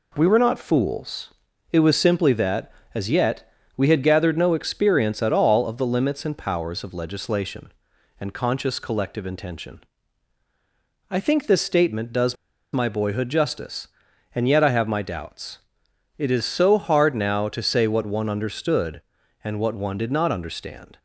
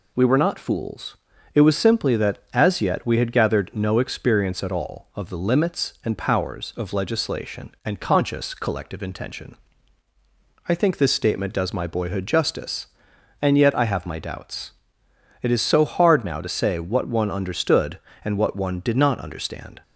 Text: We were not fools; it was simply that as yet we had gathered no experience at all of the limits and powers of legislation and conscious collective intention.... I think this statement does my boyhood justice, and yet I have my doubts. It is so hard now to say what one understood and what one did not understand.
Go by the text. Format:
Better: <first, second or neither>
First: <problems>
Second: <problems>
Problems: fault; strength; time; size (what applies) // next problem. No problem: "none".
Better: second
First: pauses between "yet" and "we"; slight; at 3.5 s; 0.26 s long // pauses between "does" and "my"; at 12.3 s; 0.38 s long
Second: none